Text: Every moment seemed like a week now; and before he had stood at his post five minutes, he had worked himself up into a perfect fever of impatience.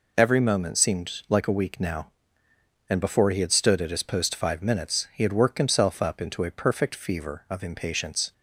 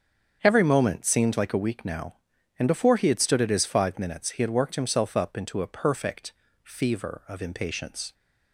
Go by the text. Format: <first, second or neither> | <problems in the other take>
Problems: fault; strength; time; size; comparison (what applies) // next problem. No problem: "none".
first | starts louder than the rest; strong; until 1.4 s; 7.5 dB // skips "post"; at 3.6 s // pauses between "perfect" and "fever"; slight; at 6.3 s; 0.32 s long